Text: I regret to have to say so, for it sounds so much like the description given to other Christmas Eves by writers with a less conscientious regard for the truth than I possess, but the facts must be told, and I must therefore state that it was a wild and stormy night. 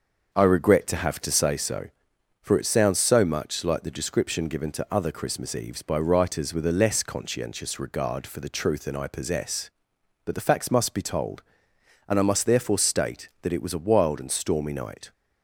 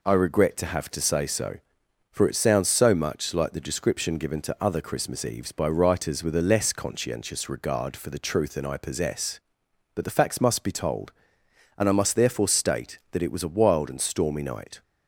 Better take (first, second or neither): second